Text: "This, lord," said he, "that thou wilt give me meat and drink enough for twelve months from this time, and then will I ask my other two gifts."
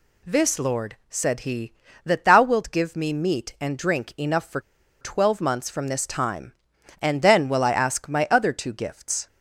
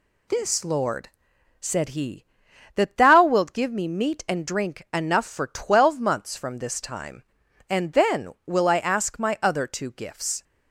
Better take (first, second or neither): second